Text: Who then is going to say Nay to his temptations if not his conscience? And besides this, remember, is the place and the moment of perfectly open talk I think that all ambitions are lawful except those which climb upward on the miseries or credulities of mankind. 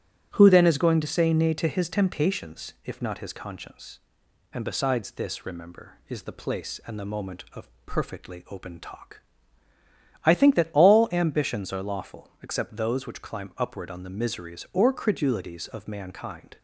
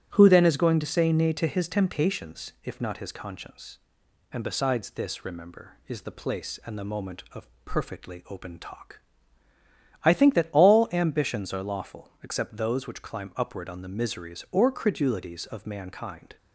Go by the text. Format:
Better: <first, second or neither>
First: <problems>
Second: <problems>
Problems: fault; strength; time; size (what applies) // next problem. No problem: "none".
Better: neither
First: starts louder than the rest; strong; until 1.3 s; 8.5 dB // pauses between "of" and "perfectly"; slight; at 7.6 s; 0.16 s long // pauses between "talk" and "I"; at 9.2 s; 1.0 s long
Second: starts louder than the rest; strong; until 1.1 s; 8.5 dB // pauses between "of" and "perfectly"; slight; at 7.4 s; 0.16 s long // pauses between "talk" and "I"; at 9.0 s; 1.0 s long